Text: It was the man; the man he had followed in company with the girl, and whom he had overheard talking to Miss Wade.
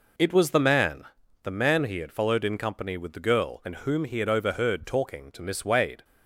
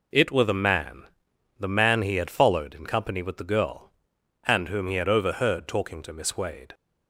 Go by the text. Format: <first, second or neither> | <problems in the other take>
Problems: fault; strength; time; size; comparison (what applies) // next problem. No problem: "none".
first | says "were" for "was"; at 0.2 s